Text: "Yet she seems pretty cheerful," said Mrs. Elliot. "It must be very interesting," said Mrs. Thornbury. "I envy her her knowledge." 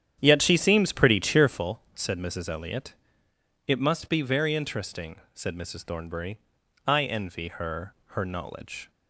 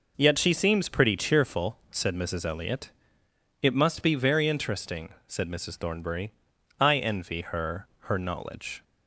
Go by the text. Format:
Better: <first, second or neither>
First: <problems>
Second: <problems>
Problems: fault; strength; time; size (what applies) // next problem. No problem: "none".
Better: second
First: starts louder than the rest; strong; until 1.6 s; 9.5 dB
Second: none